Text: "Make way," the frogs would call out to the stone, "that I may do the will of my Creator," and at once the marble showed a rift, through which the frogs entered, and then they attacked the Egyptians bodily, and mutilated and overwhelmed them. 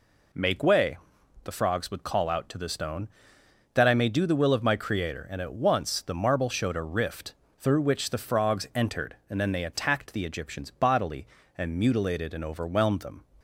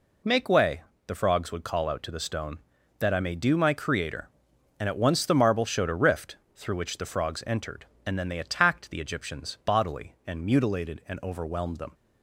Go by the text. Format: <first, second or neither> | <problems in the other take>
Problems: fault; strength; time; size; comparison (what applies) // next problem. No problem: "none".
first | skips "the will of"; at 3.5 s